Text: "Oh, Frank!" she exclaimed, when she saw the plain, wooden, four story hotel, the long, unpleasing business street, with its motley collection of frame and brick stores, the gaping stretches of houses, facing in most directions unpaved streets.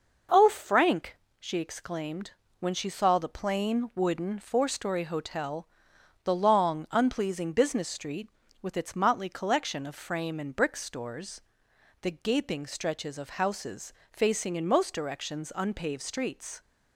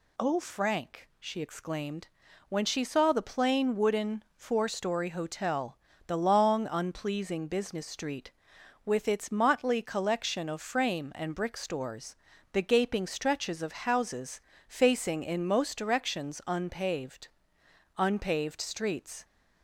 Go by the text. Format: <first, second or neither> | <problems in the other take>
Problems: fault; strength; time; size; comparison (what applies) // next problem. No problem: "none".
first | says "unpaved" twice; at 17.9 s